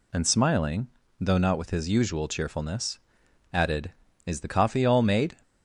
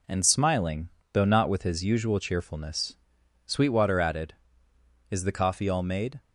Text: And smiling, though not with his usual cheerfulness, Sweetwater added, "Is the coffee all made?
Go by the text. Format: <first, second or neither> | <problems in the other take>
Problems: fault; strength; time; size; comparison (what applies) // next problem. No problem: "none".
second | skips "Sweetwater"; at 3.2 s